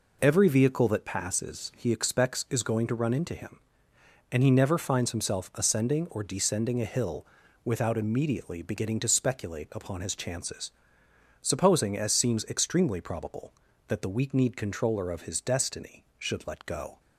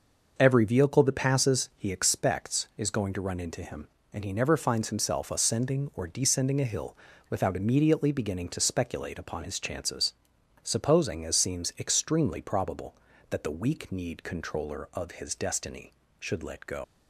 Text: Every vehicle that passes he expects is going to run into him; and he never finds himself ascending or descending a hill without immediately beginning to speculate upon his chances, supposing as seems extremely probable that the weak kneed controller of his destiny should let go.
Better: first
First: pauses between "hill" and "without"; at 7.2 s; 0.38 s long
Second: pauses between "hill" and "without"; slight; at 6.9 s; 0.36 s long // leaves "go" unfinished; at 16.8 s; 120 ms

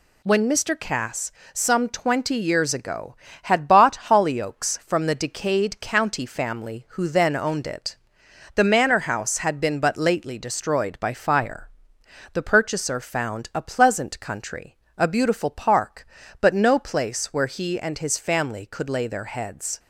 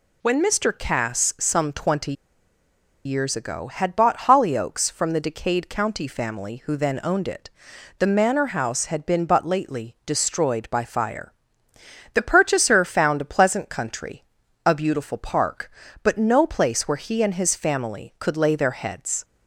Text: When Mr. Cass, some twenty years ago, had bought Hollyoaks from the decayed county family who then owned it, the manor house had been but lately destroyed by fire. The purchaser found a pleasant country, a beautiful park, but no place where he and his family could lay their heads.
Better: first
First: none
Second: pauses between "twenty" and "years"; noticeable; at 2.1 s; 0.92 s long

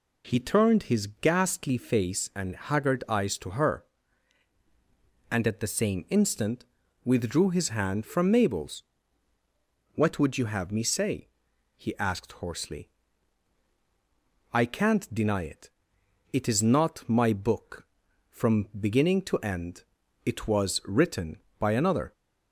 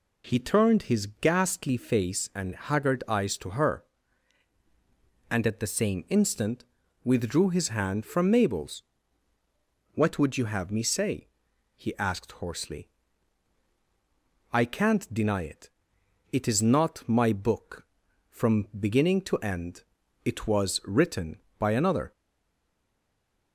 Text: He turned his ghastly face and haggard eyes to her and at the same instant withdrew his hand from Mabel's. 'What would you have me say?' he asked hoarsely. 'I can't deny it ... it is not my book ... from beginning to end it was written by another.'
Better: first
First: pauses between "his" and "ghastly"; slight; at 1.0 s; 0.16 s long // pauses between "instant" and "withdrew"; at 6.6 s; 0.40 s long // pauses between "end" and "it"; at 19.8 s; 0.40 s long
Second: pauses between "his" and "ghastly"; slight; at 1.0 s; 0.16 s long // pauses between "instant" and "withdrew"; at 6.6 s; 0.40 s long // pauses between "end" and "it"; at 19.8 s; 0.40 s long // stays silent after the last word; noticeable; from 22.1 s on; 1.4 s long

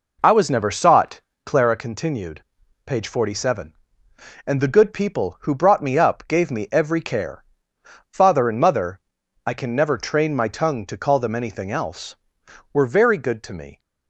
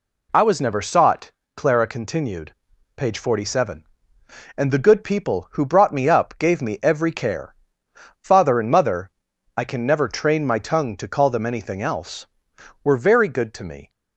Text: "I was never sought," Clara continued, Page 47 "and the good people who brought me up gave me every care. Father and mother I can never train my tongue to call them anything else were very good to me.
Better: second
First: starts louder than the rest; noticeable; until 1.7 s; 4.5 dB // pauses between "mother" and "I"; noticeable; at 8.9 s; 0.48 s long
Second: pauses between "mother" and "I"; noticeable; at 9.0 s; 0.48 s long

